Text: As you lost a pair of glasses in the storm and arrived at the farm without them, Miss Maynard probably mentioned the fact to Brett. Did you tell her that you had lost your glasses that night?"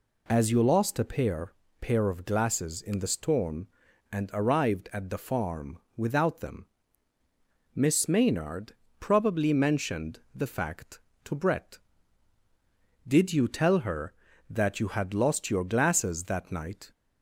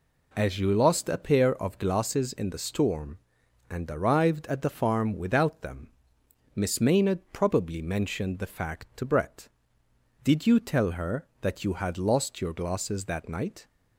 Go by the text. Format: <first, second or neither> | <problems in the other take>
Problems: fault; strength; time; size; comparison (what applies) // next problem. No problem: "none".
second | says "pair" twice; at 1.7 s // pauses between "farm" and "without"; slight; at 5.7 s; 0.16 s long // pauses between "Maynard" and "probably"; slight; at 8.7 s; 0.26 s long // pauses between "mentioned" and "the"; slight; at 10.1 s; 0.16 s long